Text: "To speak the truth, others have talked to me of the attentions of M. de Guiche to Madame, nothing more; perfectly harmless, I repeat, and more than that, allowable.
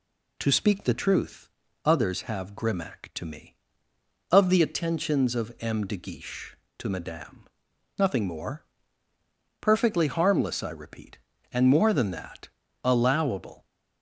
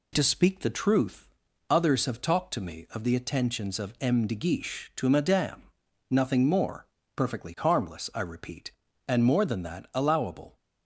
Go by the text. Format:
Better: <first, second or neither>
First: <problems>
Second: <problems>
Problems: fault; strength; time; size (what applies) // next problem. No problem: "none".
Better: second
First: says "grimac" for "talked"; at 2.5 s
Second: none